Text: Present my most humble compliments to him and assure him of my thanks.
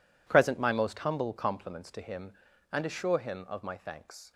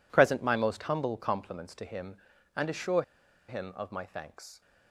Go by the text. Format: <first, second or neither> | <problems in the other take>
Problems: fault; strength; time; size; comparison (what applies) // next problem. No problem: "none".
first | pauses between "assure" and "him"; at 3.0 s; 0.45 s long